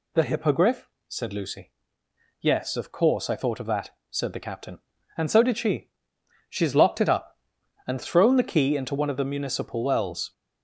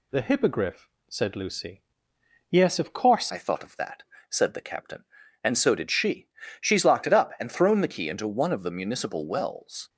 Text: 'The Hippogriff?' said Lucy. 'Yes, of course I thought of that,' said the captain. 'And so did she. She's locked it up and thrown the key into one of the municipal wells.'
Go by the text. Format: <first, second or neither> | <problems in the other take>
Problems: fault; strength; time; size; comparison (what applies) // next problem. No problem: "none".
first | changes voice at "I"; from 3.2 s on; 6.6 s long